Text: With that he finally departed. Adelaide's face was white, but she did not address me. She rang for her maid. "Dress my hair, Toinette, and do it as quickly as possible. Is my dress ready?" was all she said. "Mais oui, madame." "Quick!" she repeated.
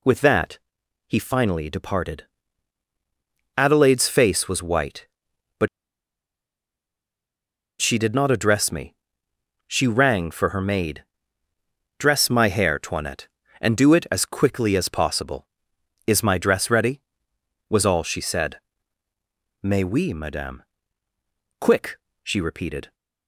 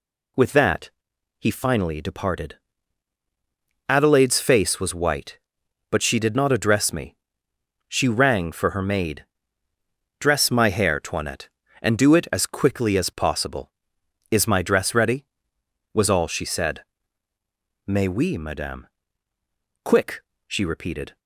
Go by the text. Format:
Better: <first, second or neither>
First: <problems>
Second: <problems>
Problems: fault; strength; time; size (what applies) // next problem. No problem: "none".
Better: second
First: pauses between "that" and "he"; noticeable; at 0.5 s; 0.50 s long // pauses between "but" and "she"; strong; at 5.6 s; 2.1 s long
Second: pauses between "that" and "he"; noticeable; at 0.8 s; 0.50 s long